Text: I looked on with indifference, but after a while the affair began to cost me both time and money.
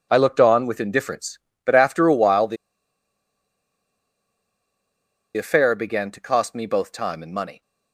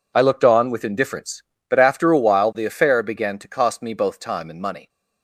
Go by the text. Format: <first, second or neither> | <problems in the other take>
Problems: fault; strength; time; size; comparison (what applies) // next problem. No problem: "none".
second | pauses between "the" and "affair"; strong; at 2.5 s; 2.8 s long